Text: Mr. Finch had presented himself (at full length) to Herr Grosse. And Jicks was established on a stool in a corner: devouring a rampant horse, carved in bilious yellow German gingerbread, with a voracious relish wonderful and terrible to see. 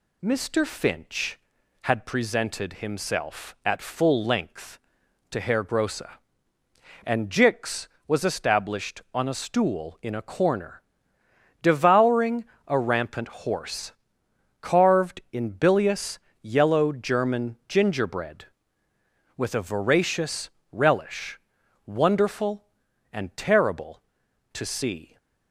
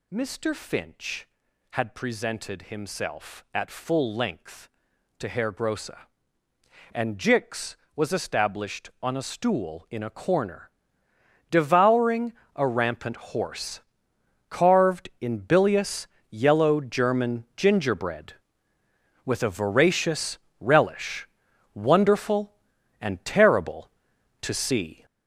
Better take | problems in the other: first | gets louder; strong; throughout; 7.5 dB // pauses between "devouring" and "a"; slight; at 12.3 s; 0.24 s long; slight in the first // pauses between "bilious" and "yellow"; slight; at 16.0 s; 0.22 s long; slight in the first // pauses between "voracious" and "relish"; slight; at 20.3 s; 0.22 s long; slight in the first // pauses between "relish" and "wonderful"; noticeable; at 21.2 s; 0.48 s long; noticeable in the first

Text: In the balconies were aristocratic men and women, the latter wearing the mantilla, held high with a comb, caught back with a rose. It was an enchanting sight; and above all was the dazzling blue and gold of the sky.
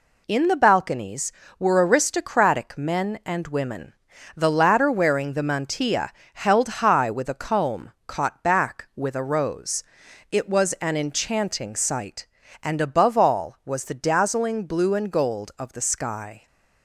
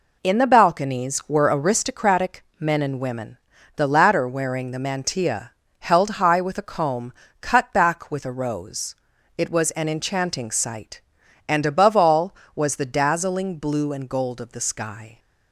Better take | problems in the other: first | pauses between "aristocratic" and "men"; slight; at 2.4 s; 0.16 s long // says "cut" for "caught"; at 7.4 s

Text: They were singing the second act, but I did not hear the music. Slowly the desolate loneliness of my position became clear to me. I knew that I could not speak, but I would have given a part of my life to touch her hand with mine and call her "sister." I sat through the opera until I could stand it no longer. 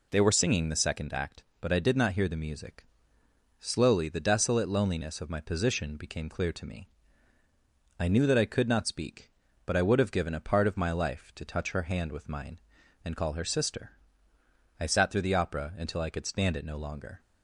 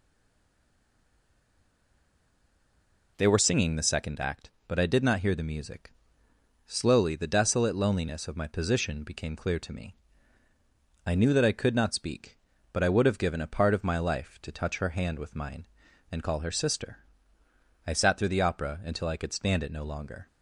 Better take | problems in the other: first | stays silent before the first word; strong; until 3.1 s; 3.1 s long

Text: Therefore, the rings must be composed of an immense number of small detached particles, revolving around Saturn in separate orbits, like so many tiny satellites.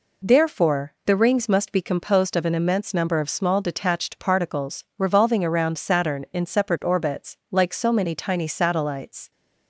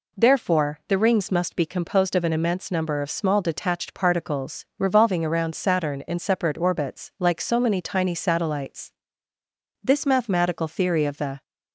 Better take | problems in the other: first | goes on to say "This mathematical theory of the"; from 9.8 s on; 1.6 s long

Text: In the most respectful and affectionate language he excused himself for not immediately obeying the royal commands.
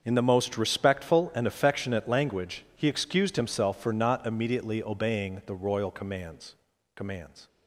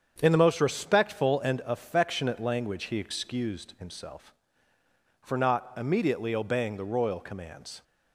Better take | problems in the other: second | starts louder than the rest; until 1.0 s; 6.5 dB; strong in the second // says "commands" twice; at 6.9 s

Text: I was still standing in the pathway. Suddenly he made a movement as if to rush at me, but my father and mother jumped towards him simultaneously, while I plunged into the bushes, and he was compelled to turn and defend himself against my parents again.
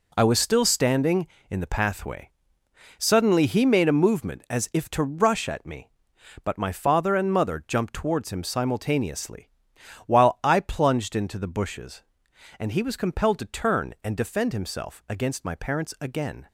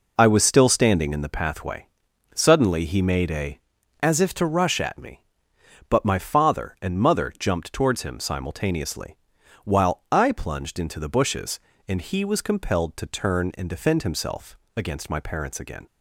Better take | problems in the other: first | skips "movement"; at 3.7 s // pauses between "himself" and "against"; slight; at 14.5 s; 0.18 s long

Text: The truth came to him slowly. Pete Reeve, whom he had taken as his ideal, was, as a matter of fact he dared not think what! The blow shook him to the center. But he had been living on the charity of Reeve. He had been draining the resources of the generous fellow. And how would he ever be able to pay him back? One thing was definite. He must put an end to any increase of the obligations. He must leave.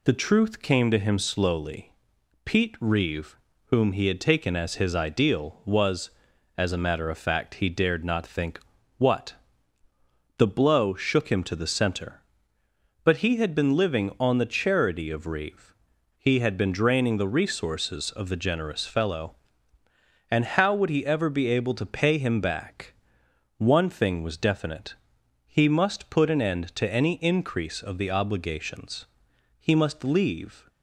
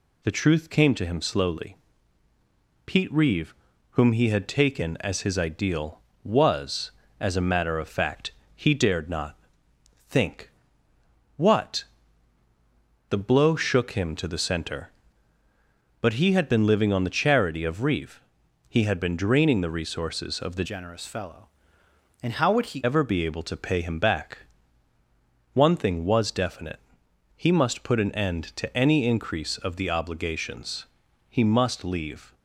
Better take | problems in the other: first | pauses between "fact" and "he"; slight; at 8.3 s; 0.22 s long // pauses between "not" and "think"; noticeable; at 9.3 s; 0.72 s long // pauses between "think" and "what"; noticeable; at 10.5 s; 0.86 s long; also in the first // changes voice from "generous" to "he"; from 20.6 to 22.8 s; 2.2 s long

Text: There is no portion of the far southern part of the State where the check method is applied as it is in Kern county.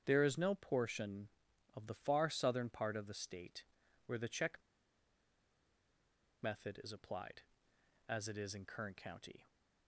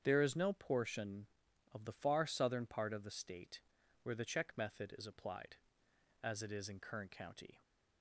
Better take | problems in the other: second | starts louder than the rest; strong; until 1.0 s; 8 dB; strong in the second // pauses between "State" and "where"; at 3.6 s; 0.42 s long; also in the second // pauses between "check" and "method"; strong; at 4.5 s; 1.8 s long

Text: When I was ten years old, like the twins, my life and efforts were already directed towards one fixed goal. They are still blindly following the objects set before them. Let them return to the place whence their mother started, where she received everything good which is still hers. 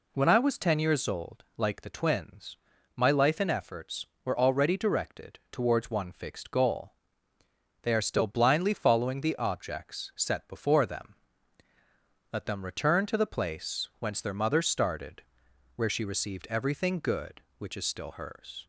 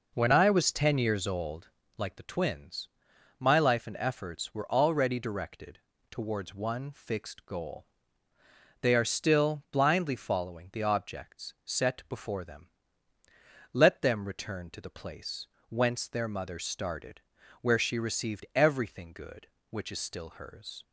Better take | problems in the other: first | starts louder than the rest; noticeable; until 1.8 s; 5 dB // pauses between "directed" and "towards"; slight; at 5.7 s; 0.32 s long // pauses between "place" and "whence"; slight; at 15.4 s; 0.22 s long

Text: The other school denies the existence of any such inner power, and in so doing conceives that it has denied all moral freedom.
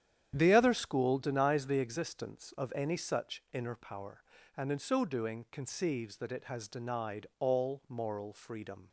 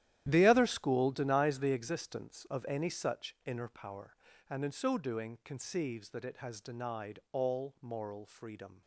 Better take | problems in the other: first | gets quieter; strong; throughout; 13.5 dB // starts louder than the rest; strong; until 1.3 s; 12 dB; strong in the first

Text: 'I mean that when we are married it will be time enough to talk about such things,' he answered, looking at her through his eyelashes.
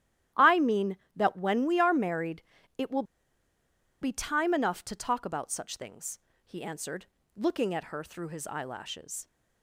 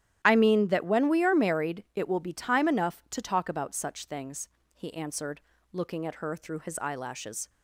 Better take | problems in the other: second | starts louder than the rest; strong; until 1.5 s; 12 dB; strong in the second // pauses between "married" and "it"; slight; at 2.4 s; 0.36 s long // pauses between "will" and "be"; at 3.0 s; 0.98 s long

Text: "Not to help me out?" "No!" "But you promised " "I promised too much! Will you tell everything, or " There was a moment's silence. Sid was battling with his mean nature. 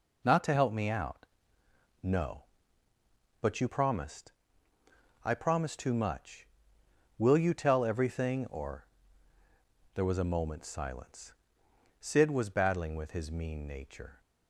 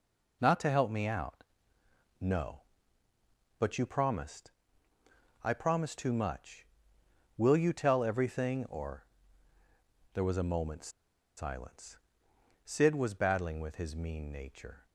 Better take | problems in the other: first | pauses between "moment's" and "silence"; noticeable; at 10.8 s; 0.47 s long

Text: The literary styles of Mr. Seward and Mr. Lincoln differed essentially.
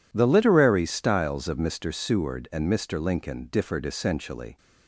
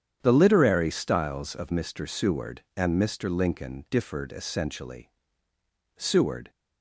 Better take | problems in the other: first | starts louder than the rest; strong; until 1.2 s; 8.5 dB // goes on to say "Seward"; from 5.9 s on; 0.54 s long

